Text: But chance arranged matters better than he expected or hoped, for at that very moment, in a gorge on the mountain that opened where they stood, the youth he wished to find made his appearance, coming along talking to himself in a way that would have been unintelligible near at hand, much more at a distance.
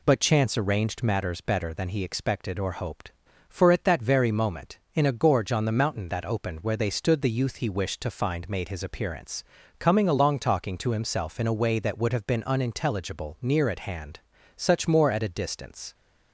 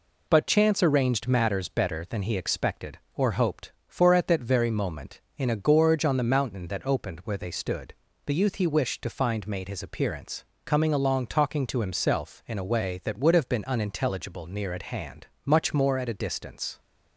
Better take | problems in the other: second | says "such" for "much"; at 14.5 s

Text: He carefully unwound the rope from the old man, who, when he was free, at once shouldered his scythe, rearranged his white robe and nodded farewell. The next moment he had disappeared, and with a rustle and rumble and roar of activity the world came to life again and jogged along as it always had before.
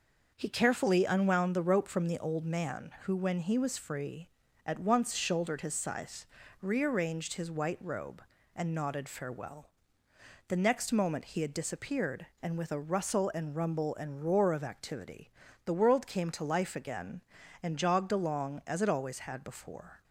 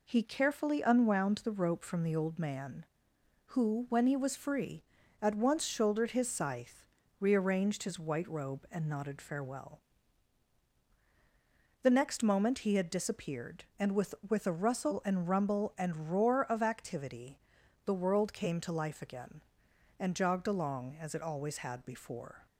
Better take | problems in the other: first | says "with" twice; at 14.2 s // pauses between "activity" and "the"; noticeable; at 17.3 s; 0.46 s long; slight in the first

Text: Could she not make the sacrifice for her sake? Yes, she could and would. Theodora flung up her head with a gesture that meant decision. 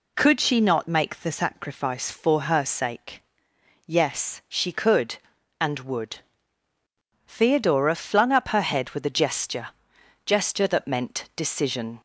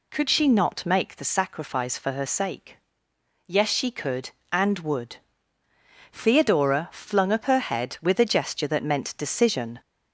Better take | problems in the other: second | says "gesture" twice; at 10.2 s

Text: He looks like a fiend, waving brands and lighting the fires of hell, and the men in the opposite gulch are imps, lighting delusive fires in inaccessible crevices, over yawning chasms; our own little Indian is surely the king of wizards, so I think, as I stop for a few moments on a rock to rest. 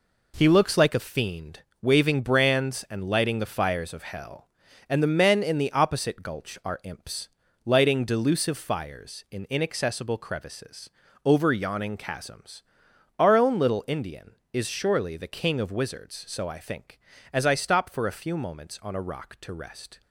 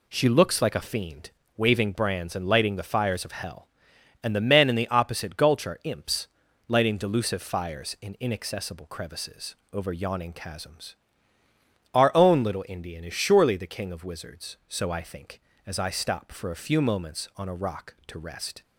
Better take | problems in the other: first | says "She" for "He"; at 0.1 s

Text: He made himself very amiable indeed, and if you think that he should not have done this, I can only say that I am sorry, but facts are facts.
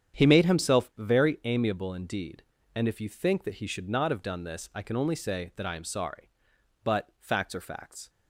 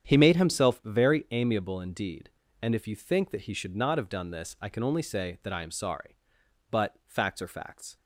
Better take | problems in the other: neither | starts louder than the rest; strong; the same in both

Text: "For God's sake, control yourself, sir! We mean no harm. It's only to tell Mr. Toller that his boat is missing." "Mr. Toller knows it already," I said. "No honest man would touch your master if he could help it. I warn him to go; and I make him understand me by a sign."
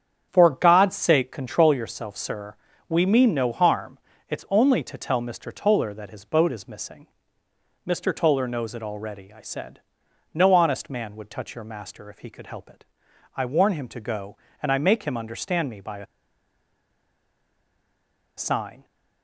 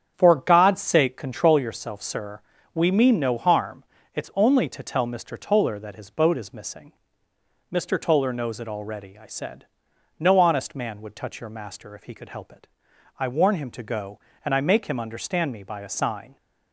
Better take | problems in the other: second | starts louder than the rest; strong; until 1.3 s; 8 dB; strong in the second // pauses between "a" and "sign"; strong; at 16.0 s; 2.3 s long

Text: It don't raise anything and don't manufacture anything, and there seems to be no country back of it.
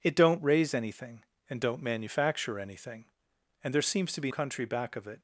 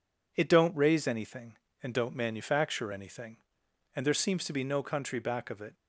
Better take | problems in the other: second | skips "no"; at 4.3 s

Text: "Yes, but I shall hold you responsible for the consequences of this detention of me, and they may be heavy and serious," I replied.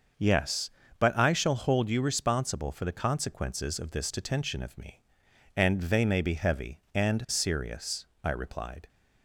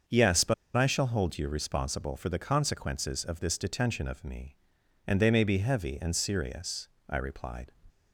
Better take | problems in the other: first | starts louder than the rest; until 1.3 s; 6.5 dB; also in the first // pauses between "but" and "I"; slight; at 0.5 s; 0.21 s long

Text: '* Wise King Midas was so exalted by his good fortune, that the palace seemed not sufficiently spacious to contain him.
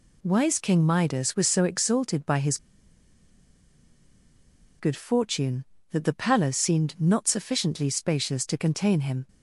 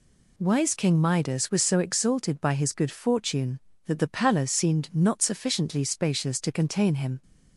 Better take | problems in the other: second | pauses between "his" and "good"; strong; at 2.5 s; 2.2 s long

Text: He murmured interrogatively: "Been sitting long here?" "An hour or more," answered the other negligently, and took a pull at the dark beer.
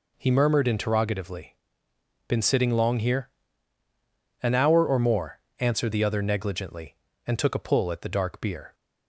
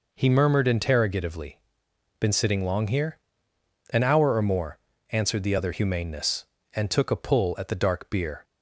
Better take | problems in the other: first | says "humaneness" for "negligently"; at 5.7 s

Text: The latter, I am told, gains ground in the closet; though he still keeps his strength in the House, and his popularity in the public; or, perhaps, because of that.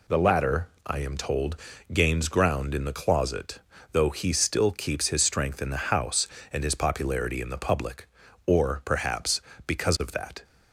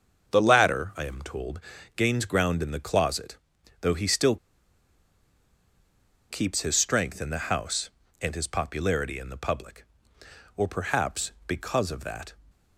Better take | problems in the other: first | starts louder than the rest; until 1.3 s; 7 dB // pauses between "still" and "keeps"; strong; at 4.3 s; 1.9 s long

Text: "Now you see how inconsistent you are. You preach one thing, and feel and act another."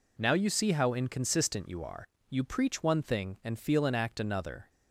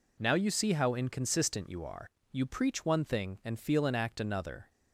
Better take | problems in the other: neither | none

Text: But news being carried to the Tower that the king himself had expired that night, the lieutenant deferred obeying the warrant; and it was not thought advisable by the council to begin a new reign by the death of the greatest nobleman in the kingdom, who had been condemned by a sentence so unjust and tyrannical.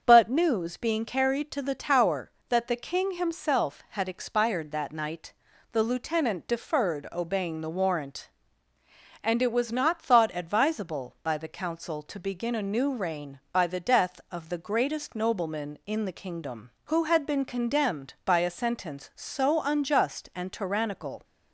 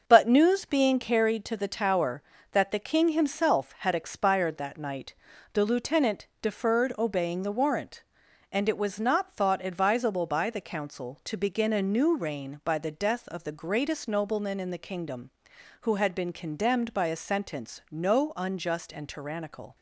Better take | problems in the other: first | starts louder than the rest; noticeable; until 1.0 s; 6 dB; also in the first // says "no" for "so"; at 17.8 s

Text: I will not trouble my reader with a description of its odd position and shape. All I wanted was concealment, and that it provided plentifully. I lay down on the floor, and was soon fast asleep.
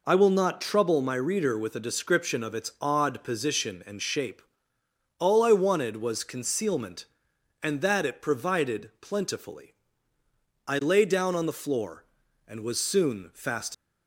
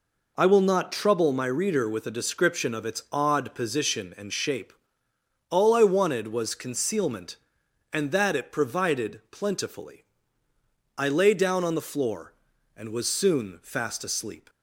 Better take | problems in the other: second | stops before "asleep"; at 13.7 s

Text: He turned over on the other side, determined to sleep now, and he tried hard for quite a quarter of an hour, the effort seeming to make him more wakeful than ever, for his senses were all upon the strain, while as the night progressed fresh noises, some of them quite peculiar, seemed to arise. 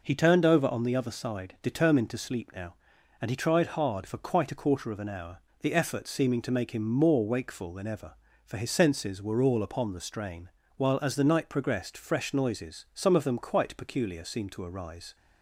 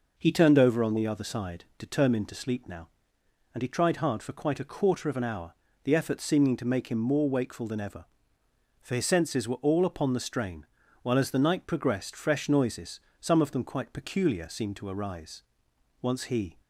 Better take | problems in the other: first | goes on to say "Once he"; from 16.0 s on; 0.56 s long

